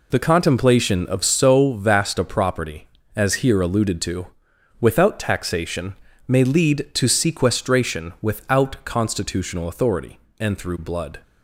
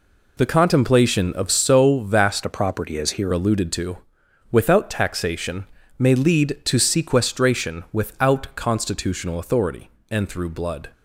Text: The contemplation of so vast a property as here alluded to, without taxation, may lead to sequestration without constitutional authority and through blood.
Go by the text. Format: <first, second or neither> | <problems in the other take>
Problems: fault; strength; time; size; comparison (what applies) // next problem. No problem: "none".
first | changes voice from "a" to "here"; from 2.4 to 3.3 s; 0.9 s long